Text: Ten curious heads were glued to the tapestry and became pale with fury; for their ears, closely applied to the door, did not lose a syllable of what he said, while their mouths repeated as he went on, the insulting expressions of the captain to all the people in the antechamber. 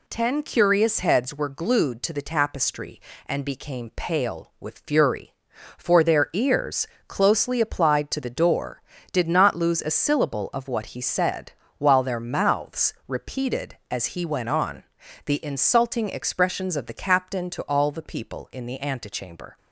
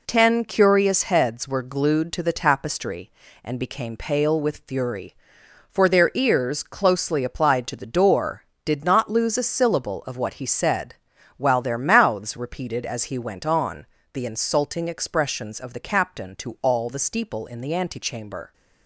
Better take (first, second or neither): first